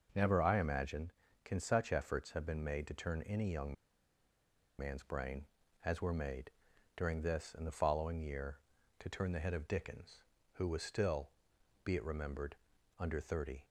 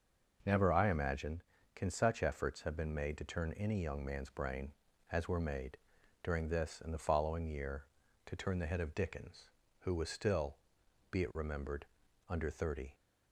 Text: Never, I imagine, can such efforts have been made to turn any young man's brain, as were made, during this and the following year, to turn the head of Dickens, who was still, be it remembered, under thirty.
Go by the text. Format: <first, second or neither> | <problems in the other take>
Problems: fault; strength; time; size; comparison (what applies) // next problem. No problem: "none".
second | pauses between "young" and "man's"; at 3.7 s; 1.0 s long